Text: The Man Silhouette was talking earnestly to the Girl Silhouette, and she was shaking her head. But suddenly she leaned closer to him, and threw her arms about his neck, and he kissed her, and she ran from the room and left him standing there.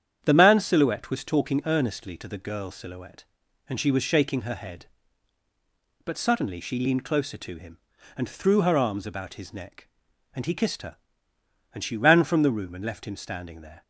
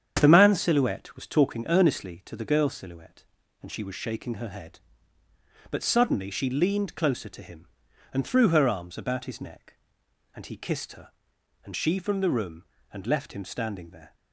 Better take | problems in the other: first | starts louder than the rest; strong; until 1.2 s; 8 dB; strong in the first // skips "ran"; at 11.9 s

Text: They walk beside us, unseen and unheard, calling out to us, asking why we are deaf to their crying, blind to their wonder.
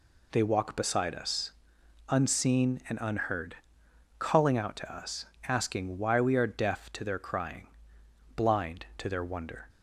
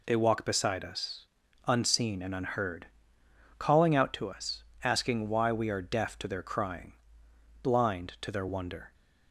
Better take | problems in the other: neither | none

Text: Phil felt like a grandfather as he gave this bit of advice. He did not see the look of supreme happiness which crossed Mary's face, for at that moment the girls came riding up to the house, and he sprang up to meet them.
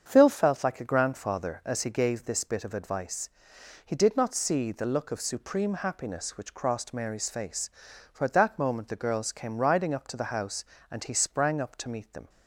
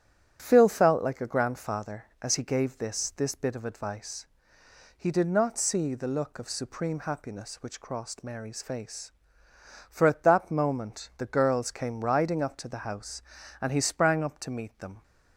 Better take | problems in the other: first | starts louder than the rest; strong; until 1.4 s; 9 dB; strong in the first // says "this" twice; at 3.1 s

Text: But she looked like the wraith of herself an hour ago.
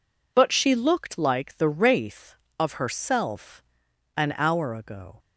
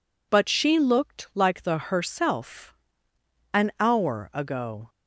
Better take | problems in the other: first | skips "wraith of"; at 1.7 s // pauses between "herself" and "an"; noticeable; at 2.7 s; 0.78 s long; noticeable in the first

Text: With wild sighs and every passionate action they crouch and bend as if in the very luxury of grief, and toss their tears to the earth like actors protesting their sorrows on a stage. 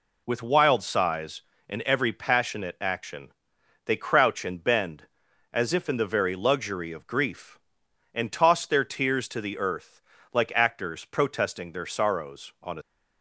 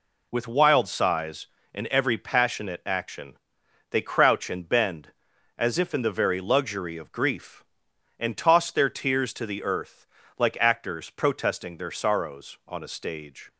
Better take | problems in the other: second | pauses between "action" and "they"; noticeable; at 3.2 s; 0.56 s long; noticeable in the second // pauses between "earth" and "like"; slight; at 10.0 s; 0.32 s long; slight in the second // stops before "stage"; at 12.8 s

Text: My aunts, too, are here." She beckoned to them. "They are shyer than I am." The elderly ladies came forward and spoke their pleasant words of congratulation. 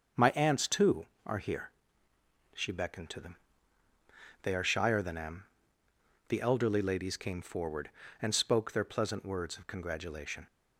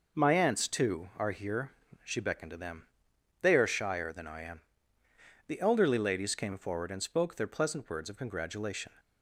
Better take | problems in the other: second | starts louder than the rest; until 1.3 s; 6.5 dB // skips "I"; at 5.1 s

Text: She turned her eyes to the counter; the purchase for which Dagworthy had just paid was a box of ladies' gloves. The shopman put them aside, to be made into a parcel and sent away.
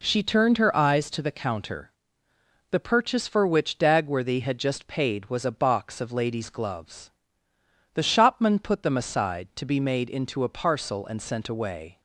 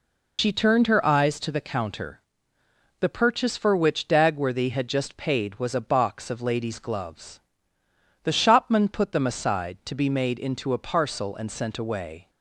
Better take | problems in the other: first | loses the start of "She"; at 0.3 s; 85 ms

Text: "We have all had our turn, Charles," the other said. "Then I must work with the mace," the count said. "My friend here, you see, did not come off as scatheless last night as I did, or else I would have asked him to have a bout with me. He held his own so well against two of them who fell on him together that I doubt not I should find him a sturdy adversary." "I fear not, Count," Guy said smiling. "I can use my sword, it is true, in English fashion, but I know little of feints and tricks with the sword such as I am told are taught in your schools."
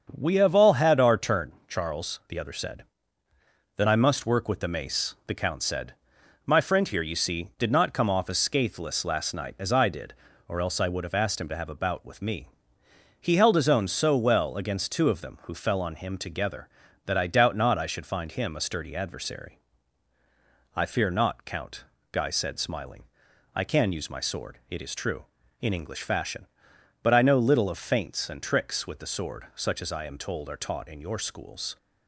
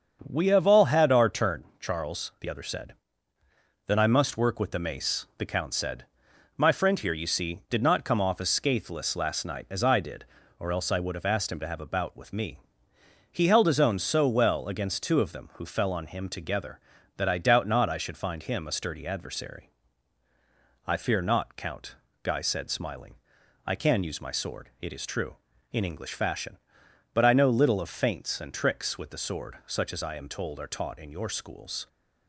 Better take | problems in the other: neither | starts louder than the rest; the same in both

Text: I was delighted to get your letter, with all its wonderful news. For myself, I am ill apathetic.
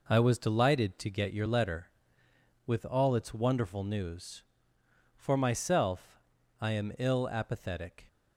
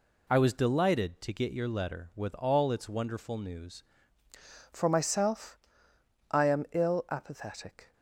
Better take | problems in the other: first | changes voice at "For"; from 4.7 s on; 3.2 s long

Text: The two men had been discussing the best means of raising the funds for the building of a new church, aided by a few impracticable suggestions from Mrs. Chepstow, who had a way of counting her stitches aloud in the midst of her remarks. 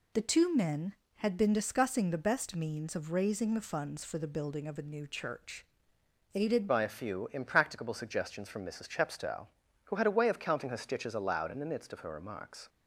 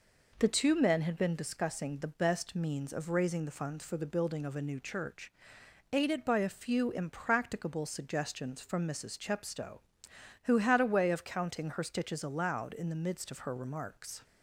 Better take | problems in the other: second | changes voice at "by"; from 6.6 s on; 6.0 s long

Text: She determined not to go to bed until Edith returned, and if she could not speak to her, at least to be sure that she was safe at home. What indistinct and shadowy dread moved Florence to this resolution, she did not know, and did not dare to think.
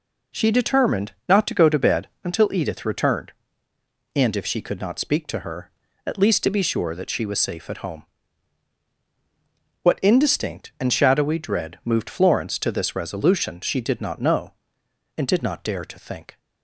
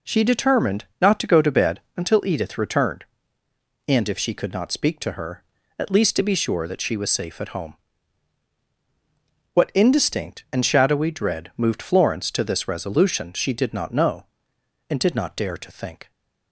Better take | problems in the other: neither | pauses between "determined" and "not"; slight; the same in both // pauses between "bed" and "until"; slight; the same in both

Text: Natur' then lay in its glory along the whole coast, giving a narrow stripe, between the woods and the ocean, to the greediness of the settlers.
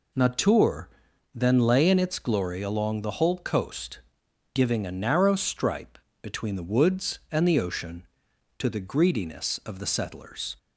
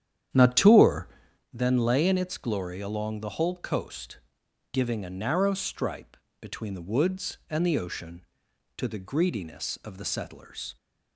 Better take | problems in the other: first | starts louder than the rest; strong; until 1.4 s; 9.5 dB // pauses between "Natur" and "then"; at 1.0 s; 0.44 s long; also in the first

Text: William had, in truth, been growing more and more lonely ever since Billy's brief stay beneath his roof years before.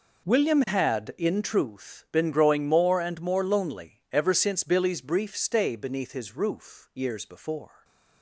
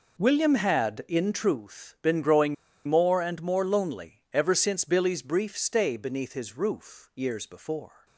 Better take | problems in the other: first | pauses between "growing" and "more"; slight; at 2.5 s; 0.32 s long

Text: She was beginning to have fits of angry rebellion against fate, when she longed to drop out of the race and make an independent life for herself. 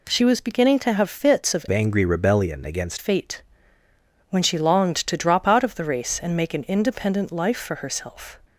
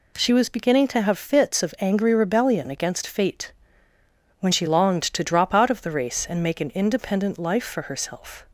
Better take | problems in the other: second | changes voice from "angry" to "against"; from 1.7 to 2.9 s; 1.2 s long

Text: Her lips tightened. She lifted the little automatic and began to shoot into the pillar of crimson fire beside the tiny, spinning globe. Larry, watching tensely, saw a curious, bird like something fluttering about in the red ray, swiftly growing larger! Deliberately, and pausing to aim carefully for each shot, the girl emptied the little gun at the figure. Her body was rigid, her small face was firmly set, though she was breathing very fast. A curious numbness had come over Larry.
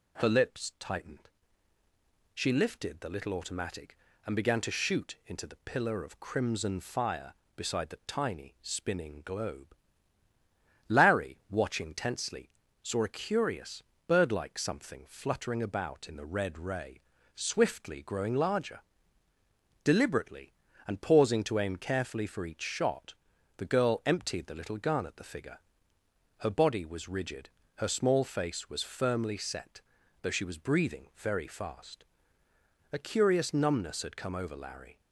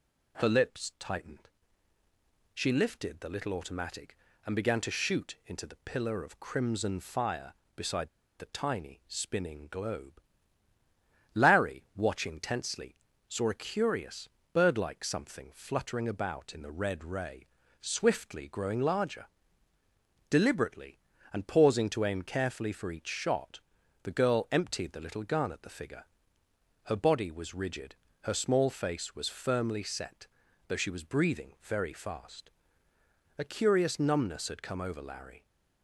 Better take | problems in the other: first | pauses between "beside" and "the"; slight; at 8.0 s; 0.30 s long

